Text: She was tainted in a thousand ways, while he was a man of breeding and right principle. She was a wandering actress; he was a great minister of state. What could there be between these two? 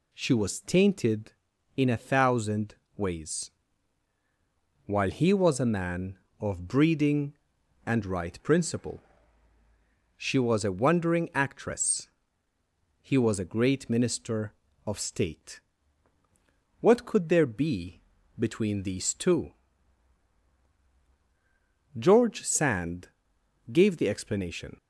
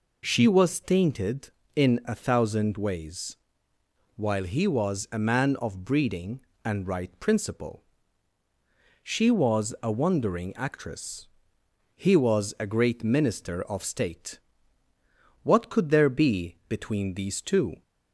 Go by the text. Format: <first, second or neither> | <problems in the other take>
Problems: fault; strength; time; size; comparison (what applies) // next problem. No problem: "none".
second | pauses between "thousand" and "ways"; slight; at 2.7 s; 0.22 s long // pauses between "be" and "between"; slight; at 18.0 s; 0.36 s long // goes on to say "George Sand gave the explanation"; strong; from 21.9 s on; 2.7 s long